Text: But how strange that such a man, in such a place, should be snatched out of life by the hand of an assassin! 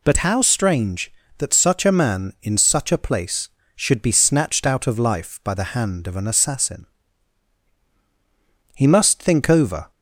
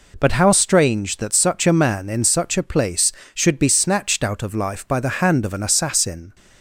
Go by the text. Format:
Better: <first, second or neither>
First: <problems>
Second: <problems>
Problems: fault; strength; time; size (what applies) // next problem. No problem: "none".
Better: second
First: goes on to say "He must think over"; noticeable; from 8.7 s on; 1.1 s long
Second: none